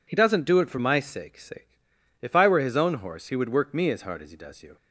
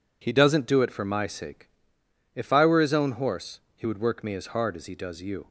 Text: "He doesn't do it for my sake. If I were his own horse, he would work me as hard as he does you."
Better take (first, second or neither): second